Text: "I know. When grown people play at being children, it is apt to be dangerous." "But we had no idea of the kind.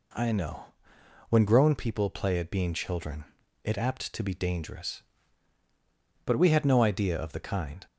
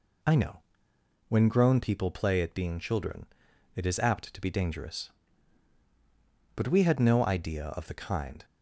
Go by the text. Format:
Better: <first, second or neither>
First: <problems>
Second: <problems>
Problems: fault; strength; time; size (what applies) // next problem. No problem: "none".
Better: second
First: skips "is"; at 3.7 s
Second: none